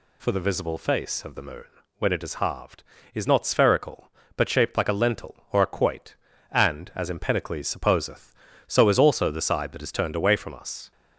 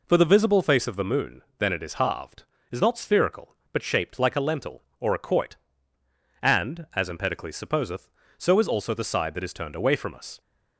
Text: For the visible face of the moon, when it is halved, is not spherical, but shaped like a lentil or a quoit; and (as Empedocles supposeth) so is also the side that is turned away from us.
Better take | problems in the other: first | says "then" for "when"; at 1.5 s

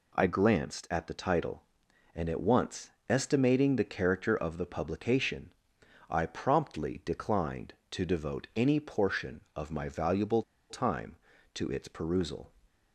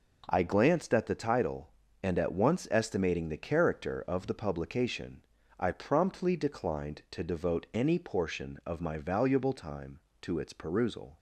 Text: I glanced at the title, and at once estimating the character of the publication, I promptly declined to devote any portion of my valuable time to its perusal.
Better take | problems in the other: second | pauses between "once" and "estimating"; slight; at 2.8 s; 0.20 s long // pauses between "valuable" and "time"; slight; at 10.4 s; 0.26 s long

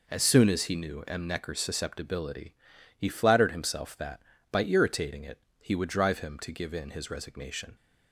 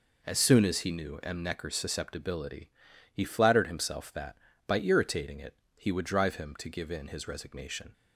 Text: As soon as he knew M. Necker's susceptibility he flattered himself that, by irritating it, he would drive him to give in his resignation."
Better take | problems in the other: neither | pauses between "susceptibility" and "he"; noticeable; the same in both

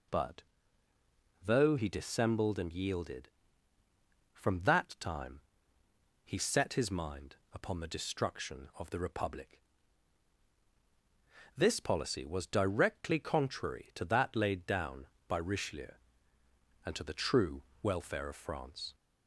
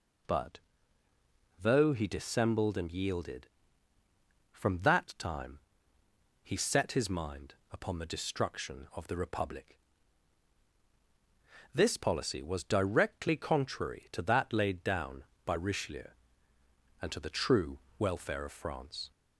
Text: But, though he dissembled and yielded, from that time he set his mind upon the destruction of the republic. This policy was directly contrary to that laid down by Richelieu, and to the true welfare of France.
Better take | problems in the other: neither | pauses between "time" and "he"; noticeable; the same in both // pauses between "mind" and "upon"; slight; the same in both // pauses between "true" and "welfare"; slight; the same in both

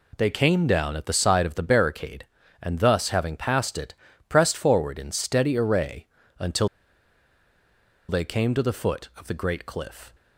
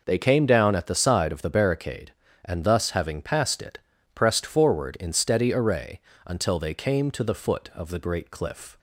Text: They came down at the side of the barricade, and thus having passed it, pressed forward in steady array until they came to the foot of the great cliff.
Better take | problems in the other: second | pauses between "array" and "until"; slight; at 6.0 s; 0.32 s long; slight in the second // pauses between "until" and "they"; strong; at 6.6 s; 1.4 s long

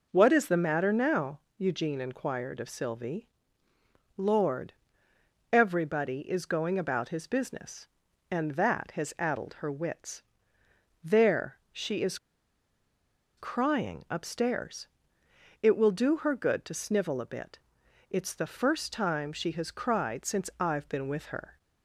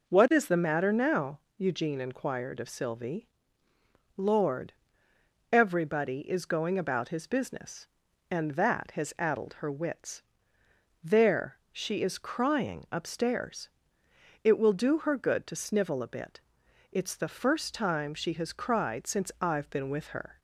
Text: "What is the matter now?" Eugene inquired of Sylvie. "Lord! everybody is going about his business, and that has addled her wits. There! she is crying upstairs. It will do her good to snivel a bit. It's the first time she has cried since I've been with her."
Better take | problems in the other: second | pauses between "is" and "crying"; at 12.1 s; 1.2 s long

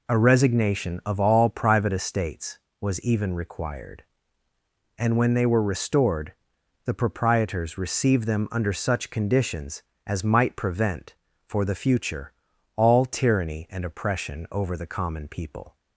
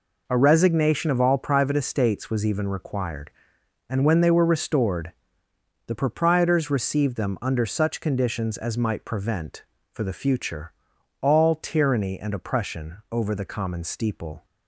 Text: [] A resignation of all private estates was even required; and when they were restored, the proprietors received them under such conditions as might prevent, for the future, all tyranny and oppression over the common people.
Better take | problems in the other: first | says "steeple" for "people"; at 13.8 s

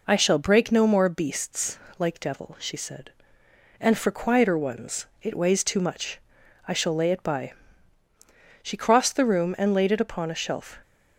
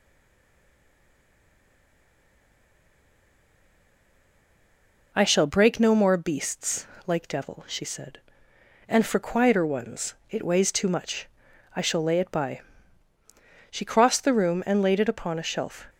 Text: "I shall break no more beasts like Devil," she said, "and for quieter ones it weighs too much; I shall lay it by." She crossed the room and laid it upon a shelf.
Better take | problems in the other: first | stays silent before the first word; strong; until 5.1 s; 5.1 s long // pauses between "beasts" and "like"; slight; at 6.8 s; 0.18 s long; slight in the first // pauses between "ones" and "it"; slight; at 10.1 s; 0.16 s long; slight in the first

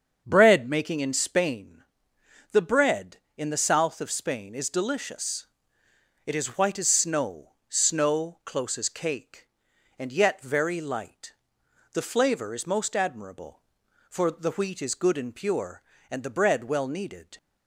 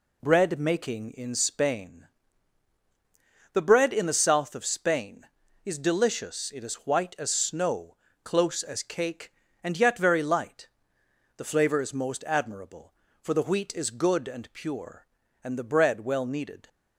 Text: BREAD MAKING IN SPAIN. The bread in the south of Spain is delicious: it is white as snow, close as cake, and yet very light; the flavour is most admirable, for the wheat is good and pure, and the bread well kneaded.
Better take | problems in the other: second | starts louder than the rest; until 1.2 s; 7 dB // says "snow" twice; at 7.6 s

